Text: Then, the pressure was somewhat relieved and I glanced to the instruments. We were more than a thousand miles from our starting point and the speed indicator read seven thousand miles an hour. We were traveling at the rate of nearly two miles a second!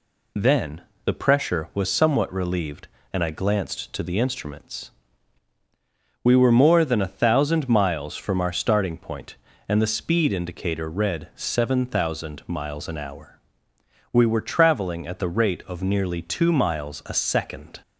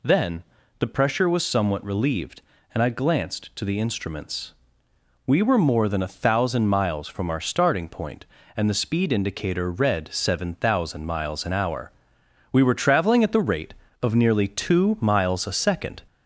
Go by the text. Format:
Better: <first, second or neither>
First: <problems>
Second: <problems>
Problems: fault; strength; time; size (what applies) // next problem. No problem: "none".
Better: first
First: none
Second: gets louder; slight; throughout; 3 dB